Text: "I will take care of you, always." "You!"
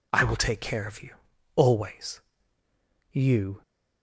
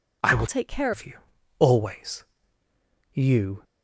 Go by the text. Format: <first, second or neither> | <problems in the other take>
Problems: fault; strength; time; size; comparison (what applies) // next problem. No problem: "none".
first | changes voice from "take" to "care"; from 0.4 to 0.9 s; 0.5 s long